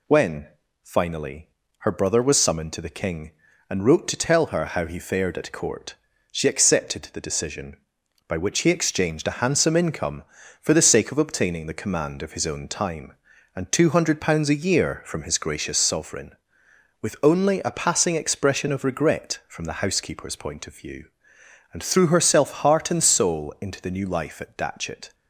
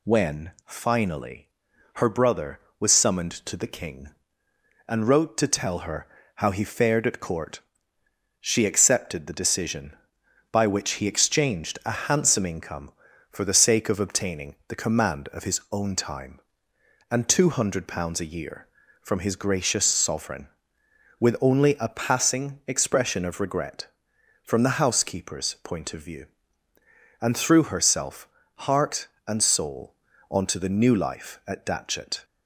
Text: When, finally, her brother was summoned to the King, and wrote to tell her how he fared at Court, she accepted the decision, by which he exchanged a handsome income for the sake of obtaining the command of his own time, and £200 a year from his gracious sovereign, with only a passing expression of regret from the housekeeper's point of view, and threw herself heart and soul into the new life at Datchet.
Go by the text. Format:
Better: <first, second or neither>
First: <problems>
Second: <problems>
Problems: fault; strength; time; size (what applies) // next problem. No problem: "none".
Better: first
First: none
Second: pauses between "her" and "how"; slight; at 6.0 s; 0.30 s long // pauses between "herself" and "heart"; slight; at 28.2 s; 0.30 s long // says "onto" for "into"; at 30.2 s